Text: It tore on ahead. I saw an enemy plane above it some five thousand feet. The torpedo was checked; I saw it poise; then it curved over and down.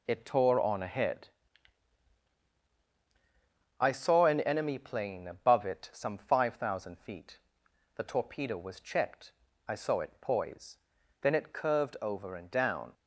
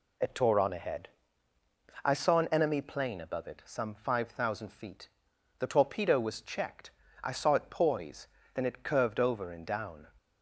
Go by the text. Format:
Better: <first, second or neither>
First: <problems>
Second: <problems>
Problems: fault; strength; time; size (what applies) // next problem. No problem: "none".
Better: neither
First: none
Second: none